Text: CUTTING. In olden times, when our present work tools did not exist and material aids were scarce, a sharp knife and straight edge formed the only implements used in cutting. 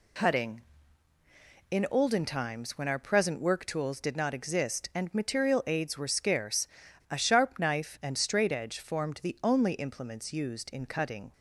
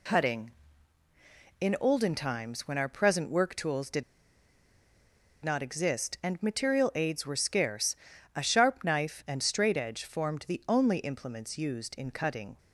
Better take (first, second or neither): first